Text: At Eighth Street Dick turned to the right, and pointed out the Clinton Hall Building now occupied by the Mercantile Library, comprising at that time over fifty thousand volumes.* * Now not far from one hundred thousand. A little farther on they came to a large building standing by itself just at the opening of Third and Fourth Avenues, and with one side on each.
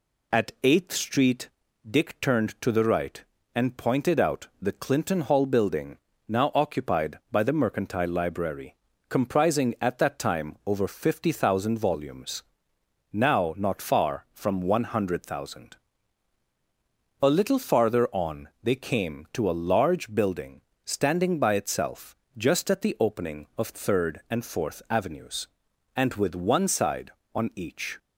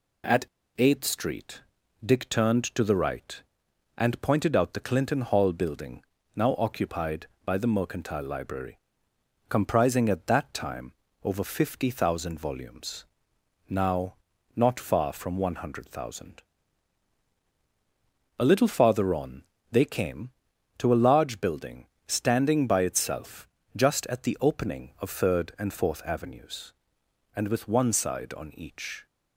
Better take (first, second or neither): first